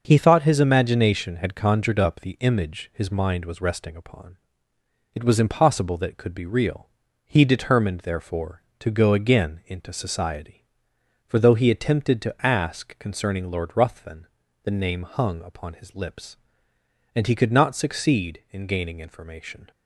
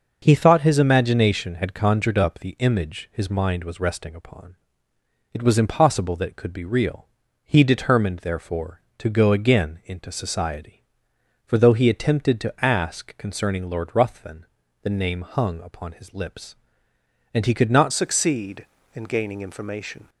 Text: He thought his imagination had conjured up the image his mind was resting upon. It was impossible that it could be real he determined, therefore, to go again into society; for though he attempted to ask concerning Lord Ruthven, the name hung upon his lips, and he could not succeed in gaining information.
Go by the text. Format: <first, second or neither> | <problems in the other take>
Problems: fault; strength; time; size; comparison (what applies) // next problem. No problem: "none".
first | pauses between "real" and "he"; slight; at 7.0 s; 0.36 s long; slight in the first // changes voice at "succeed"; from 17.9 s on; 2.1 s long